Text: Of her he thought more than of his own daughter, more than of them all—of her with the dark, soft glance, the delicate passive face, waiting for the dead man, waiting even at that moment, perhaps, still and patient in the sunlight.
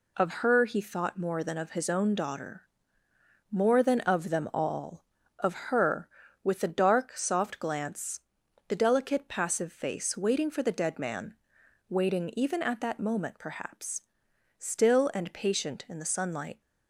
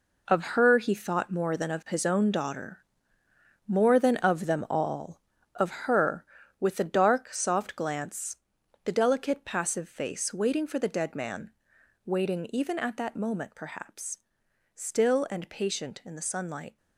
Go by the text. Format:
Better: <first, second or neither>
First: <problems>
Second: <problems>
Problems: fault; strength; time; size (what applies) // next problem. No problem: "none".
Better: first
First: none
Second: gets quieter; strong; throughout; 9.5 dB